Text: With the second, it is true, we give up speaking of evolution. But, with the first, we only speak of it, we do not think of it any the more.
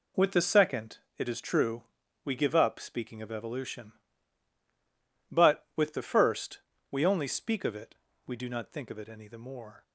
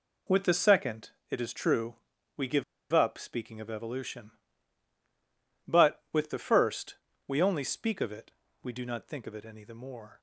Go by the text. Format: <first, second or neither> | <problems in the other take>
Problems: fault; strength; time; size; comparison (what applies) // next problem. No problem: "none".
first | pauses between "give" and "up"; slight; at 2.6 s; 0.29 s long